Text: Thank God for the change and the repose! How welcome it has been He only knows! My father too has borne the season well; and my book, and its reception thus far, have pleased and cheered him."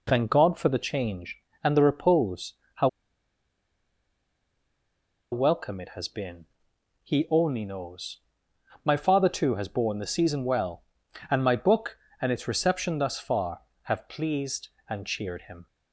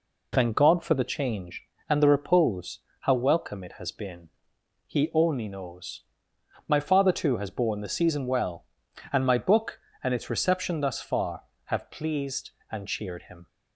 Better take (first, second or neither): second